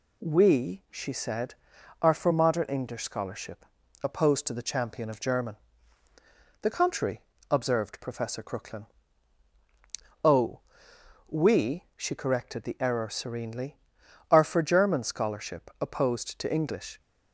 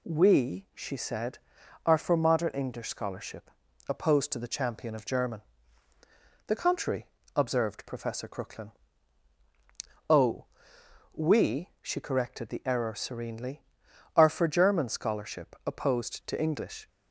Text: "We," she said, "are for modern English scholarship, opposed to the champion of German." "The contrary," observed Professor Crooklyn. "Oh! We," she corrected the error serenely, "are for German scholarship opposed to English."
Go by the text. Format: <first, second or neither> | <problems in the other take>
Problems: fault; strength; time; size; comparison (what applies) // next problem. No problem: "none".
neither | none